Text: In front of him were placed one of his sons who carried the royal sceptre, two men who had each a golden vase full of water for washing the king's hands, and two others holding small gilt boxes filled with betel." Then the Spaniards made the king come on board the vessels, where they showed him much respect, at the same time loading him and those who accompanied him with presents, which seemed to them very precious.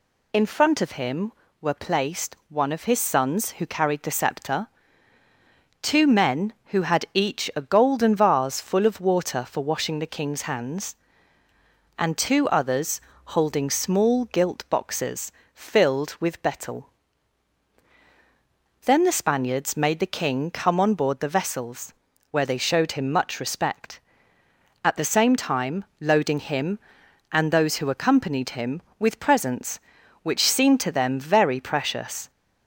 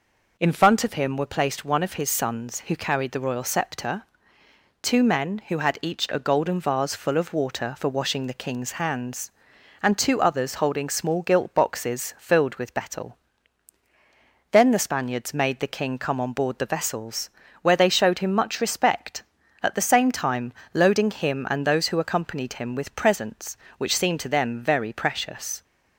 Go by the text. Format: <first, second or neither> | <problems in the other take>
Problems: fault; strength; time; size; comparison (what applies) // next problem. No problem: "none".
second | skips "royal"; at 4.0 s // pauses between "others" and "holding"; slight; at 12.9 s; 0.26 s long // pauses between "boxes" and "filled"; slight; at 15.3 s; 0.22 s long // pauses between "time" and "loading"; slight; at 25.8 s; 0.16 s long; slight in the second